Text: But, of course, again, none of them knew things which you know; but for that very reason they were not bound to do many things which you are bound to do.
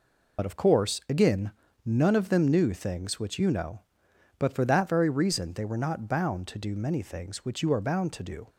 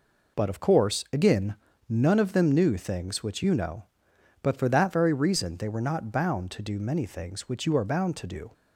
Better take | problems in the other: second | loses the start of "But"; at 0.3 s; 65 ms

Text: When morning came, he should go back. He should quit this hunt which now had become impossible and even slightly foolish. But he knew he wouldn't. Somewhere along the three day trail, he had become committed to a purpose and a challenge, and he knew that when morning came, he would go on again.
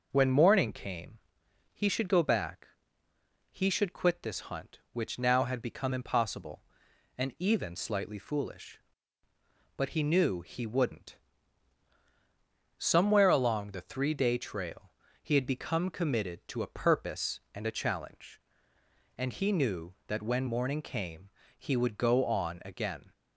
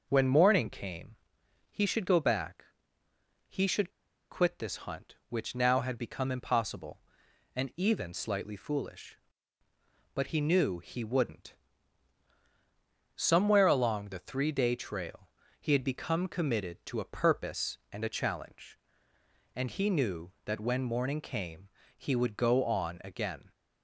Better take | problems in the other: first | pauses between "should" and "quit"; at 3.8 s; 0.40 s long

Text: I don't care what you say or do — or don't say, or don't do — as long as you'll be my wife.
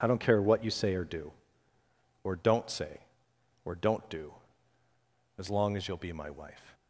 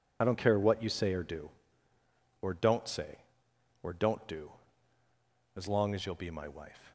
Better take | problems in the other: first | loses the start of "I"; at 0.2 s; 25 ms

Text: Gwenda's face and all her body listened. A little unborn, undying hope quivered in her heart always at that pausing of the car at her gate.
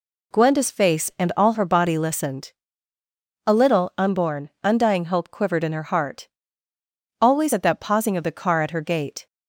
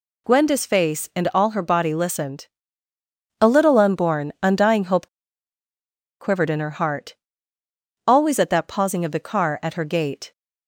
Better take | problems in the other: first | pauses between "hope" and "quivered"; at 5.0 s; 1.1 s long // pauses between "heart" and "always"; noticeable; at 7.1 s; 0.92 s long; noticeable in the first

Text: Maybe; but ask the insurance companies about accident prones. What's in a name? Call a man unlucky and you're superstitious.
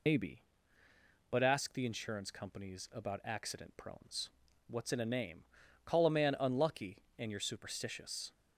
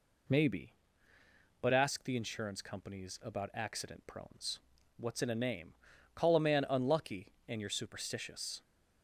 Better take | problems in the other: second | loses the start of "Maybe"; at 0.0 s; 80 ms

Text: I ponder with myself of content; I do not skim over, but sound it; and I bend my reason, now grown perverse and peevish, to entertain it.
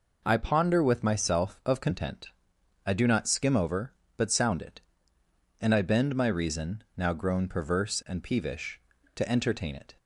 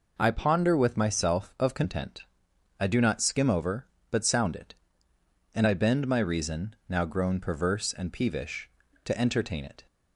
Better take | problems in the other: neither | none

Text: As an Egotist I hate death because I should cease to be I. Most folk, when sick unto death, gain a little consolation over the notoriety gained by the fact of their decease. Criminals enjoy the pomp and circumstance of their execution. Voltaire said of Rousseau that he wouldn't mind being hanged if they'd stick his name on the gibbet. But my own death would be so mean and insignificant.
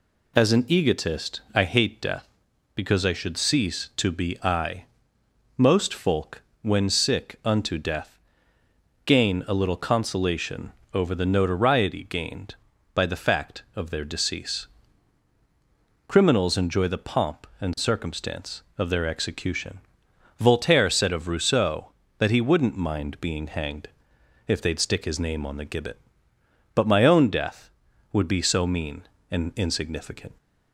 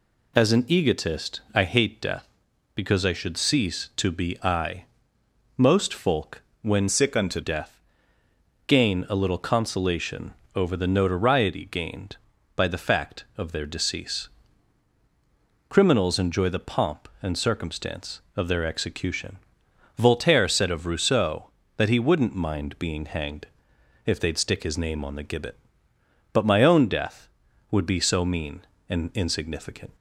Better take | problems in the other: first | changes voice from "sick" to "unto"; from 6.8 to 7.3 s; 0.5 s long // pauses between "consolation" and "over"; slight; at 10.3 s; 0.20 s long; slight in the first // pauses between "hanged" and "if"; noticeable; at 23.4 s; 0.58 s long; noticeable in the first

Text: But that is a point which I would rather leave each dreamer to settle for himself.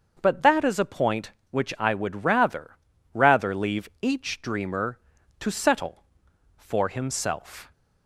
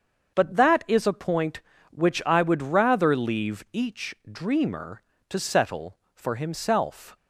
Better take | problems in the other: second | starts louder than the rest; until 1.2 s; 6.5 dB; also in the second // says "rather" twice; at 3.1 s

